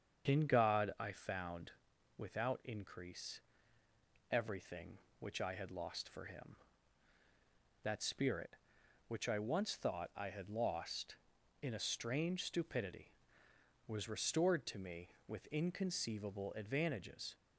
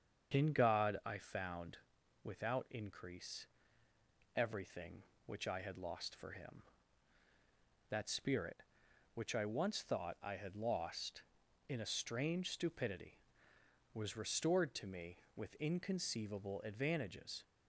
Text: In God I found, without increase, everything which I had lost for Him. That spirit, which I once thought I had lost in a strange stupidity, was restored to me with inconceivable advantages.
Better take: neither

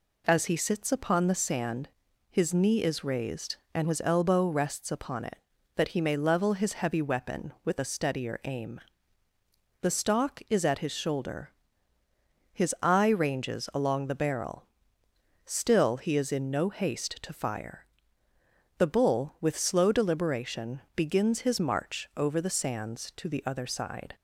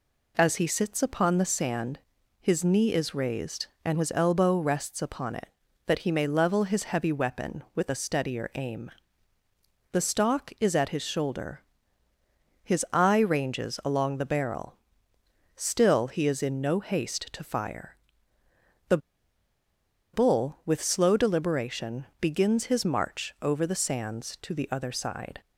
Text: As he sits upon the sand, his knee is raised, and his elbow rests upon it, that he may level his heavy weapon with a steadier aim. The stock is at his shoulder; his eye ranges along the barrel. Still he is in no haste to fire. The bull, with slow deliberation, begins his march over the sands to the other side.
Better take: first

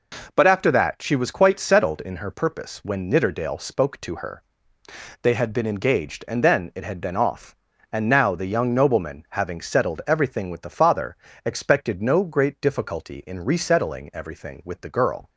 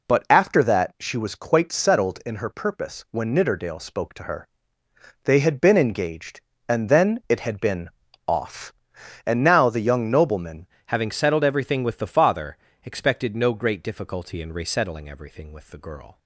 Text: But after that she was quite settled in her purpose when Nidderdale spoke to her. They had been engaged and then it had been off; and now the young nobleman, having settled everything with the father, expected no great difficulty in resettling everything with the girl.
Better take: first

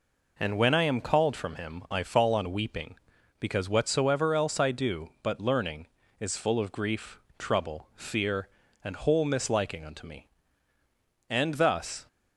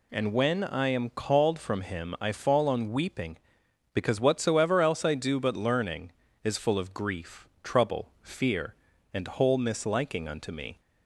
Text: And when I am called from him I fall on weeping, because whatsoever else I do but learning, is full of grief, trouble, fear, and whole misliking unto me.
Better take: second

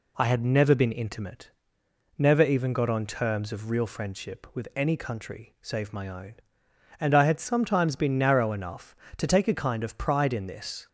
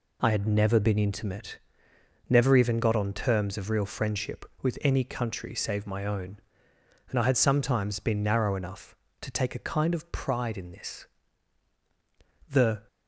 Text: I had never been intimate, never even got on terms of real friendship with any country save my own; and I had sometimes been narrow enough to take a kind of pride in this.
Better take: first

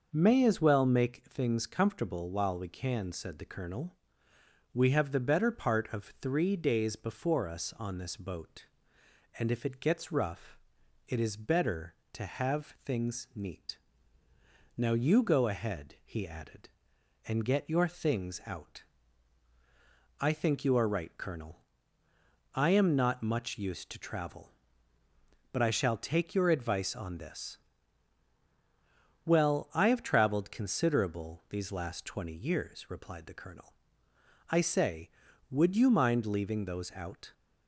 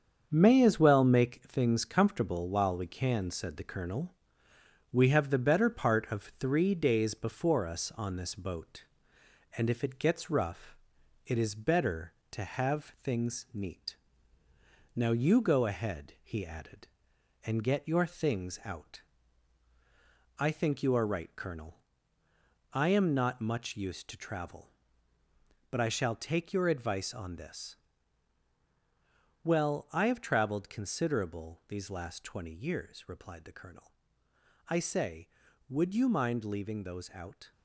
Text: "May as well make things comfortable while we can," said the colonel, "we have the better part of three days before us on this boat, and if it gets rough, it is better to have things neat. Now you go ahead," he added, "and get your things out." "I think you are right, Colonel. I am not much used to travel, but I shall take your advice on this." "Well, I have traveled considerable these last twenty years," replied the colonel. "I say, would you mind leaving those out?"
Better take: first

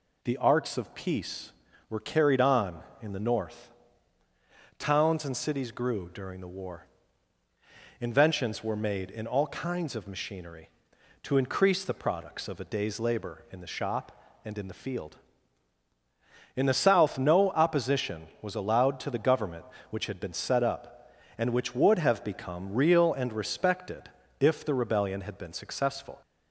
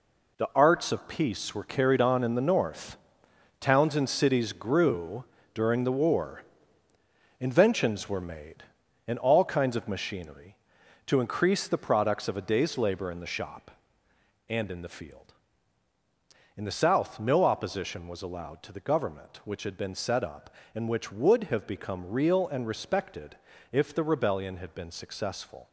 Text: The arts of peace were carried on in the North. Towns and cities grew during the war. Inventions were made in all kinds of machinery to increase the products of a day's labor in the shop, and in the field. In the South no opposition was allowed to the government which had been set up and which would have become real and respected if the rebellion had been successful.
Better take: first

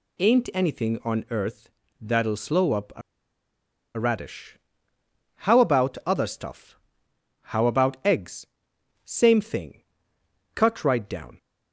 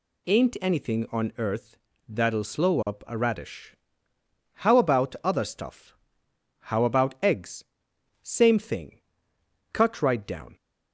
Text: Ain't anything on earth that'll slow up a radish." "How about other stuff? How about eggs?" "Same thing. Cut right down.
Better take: second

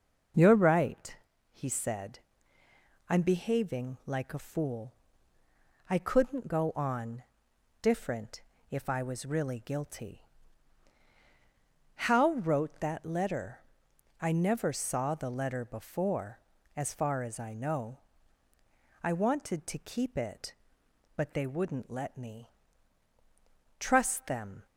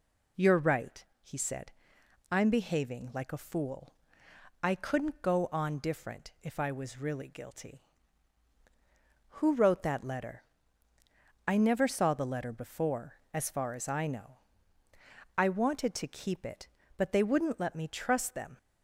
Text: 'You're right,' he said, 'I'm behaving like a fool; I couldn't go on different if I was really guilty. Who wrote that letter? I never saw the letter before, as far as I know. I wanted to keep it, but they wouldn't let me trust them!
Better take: second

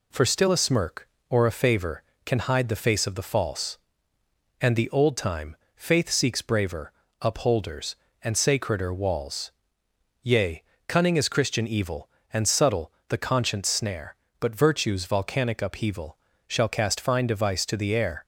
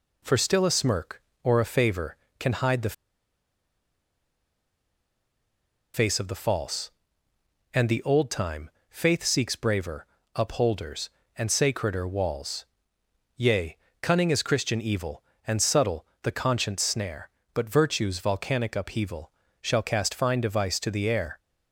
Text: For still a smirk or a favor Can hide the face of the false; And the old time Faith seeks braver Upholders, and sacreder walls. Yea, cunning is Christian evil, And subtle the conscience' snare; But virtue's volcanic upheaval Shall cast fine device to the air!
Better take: first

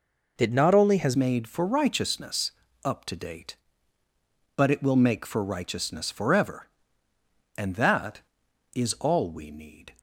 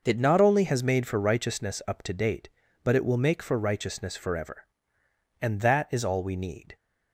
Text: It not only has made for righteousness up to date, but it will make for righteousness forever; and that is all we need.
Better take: second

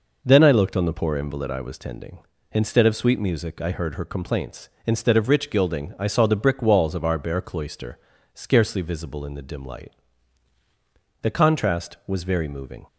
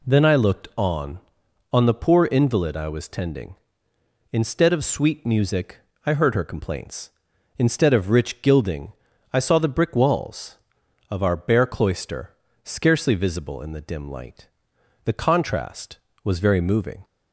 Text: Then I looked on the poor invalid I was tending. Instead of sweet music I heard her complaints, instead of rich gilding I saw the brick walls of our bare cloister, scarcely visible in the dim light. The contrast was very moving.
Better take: first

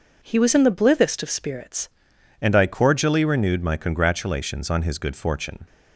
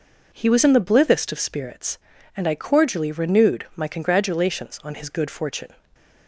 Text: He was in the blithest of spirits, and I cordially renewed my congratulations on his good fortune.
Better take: second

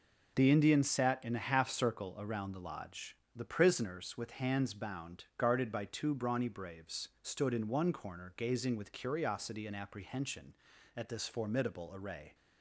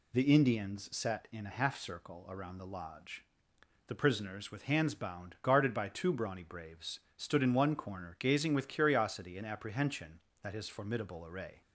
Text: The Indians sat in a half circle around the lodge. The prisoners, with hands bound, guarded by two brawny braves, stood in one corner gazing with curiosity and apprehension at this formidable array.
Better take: first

